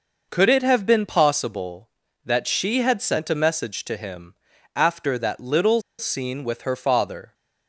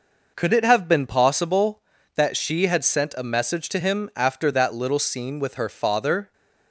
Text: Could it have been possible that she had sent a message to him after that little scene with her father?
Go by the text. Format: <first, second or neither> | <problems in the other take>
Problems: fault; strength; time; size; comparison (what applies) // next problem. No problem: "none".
second | pauses between "him" and "after"; at 4.3 s; 0.40 s long // pauses between "little" and "scene"; slight; at 5.8 s; 0.18 s long